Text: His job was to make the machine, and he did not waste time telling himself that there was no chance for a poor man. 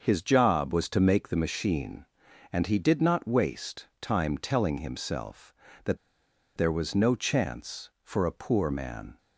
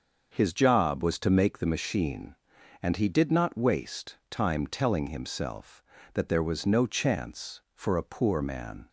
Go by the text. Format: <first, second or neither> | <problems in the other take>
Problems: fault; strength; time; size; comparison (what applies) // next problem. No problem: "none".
second | starts louder than the rest; until 1.0 s; 6 dB; also in the second // pauses between "waste" and "time"; slight; at 3.8 s; 0.16 s long; slight in the second // pauses between "that" and "there"; noticeable; at 5.9 s; 0.59 s long